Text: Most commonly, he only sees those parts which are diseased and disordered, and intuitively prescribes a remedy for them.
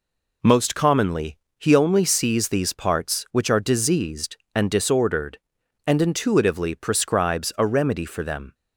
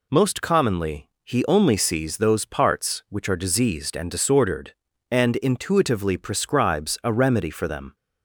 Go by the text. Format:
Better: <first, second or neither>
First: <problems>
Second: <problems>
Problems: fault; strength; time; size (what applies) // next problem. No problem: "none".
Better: second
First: says "these" for "those"; at 2.4 s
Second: none